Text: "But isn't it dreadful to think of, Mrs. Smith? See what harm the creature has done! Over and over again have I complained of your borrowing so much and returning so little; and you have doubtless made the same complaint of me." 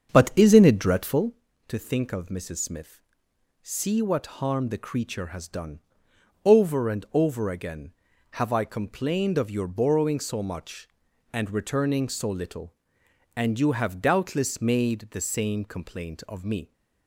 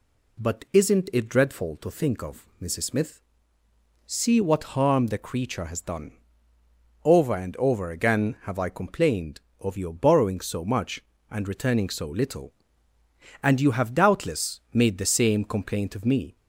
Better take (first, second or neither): second